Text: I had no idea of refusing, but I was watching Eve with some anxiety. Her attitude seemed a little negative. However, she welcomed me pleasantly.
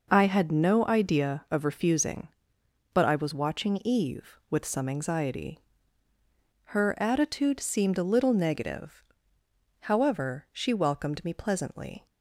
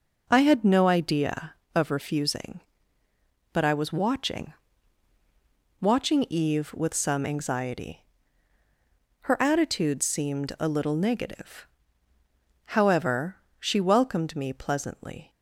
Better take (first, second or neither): first